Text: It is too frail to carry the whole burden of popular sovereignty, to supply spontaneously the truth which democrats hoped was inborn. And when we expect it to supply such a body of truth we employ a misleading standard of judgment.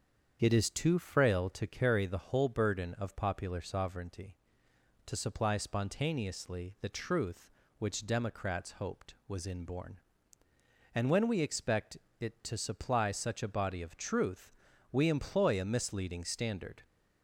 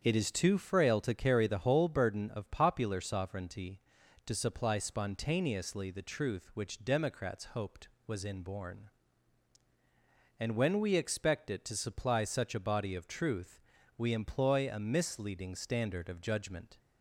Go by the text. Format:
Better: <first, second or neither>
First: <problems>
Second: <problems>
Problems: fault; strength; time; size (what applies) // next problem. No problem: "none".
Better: second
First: starts louder than the rest; strong; until 1.4 s; 7.5 dB // pauses between "expect" and "it"; slight; at 11.9 s; 0.20 s long // pauses between "truth" and "we"; at 14.5 s; 0.42 s long // stops before "of judgment"; at 16.8 s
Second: starts louder than the rest; strong; until 1.0 s; 7.5 dB // pauses between "truth" and "we"; at 13.6 s; 0.38 s long